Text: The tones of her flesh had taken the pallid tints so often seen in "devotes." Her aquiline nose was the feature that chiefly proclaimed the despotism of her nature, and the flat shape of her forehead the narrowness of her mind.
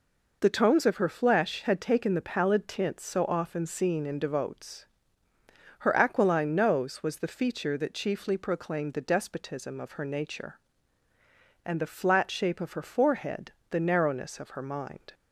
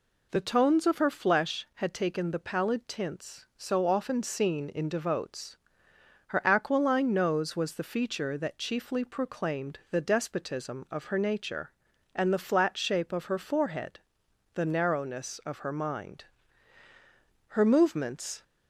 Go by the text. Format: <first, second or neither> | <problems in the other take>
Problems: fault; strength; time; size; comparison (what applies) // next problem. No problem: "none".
first | pauses between "forehead" and "the"; noticeable; at 14.0 s; 0.54 s long; slight in the first // goes on to say "Her movements"; noticeable; from 17.5 s on; 0.88 s long